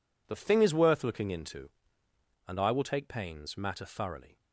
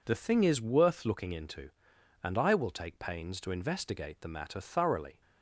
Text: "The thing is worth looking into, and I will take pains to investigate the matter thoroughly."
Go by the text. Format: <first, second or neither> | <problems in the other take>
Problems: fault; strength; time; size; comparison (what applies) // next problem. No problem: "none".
second | skips "to investigate the"; at 3.5 s